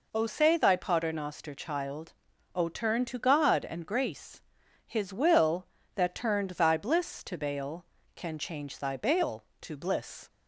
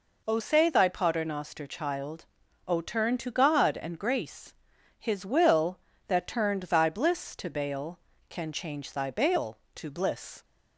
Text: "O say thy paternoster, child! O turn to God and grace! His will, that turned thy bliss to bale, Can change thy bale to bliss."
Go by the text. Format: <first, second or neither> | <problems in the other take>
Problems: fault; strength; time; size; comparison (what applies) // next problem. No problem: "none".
neither | none